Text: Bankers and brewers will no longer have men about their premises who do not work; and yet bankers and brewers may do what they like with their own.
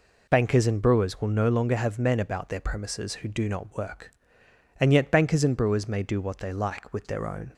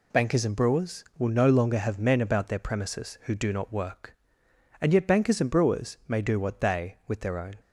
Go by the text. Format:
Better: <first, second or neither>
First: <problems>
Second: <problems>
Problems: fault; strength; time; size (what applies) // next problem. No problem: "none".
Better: first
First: none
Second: skips "like"; at 7.0 s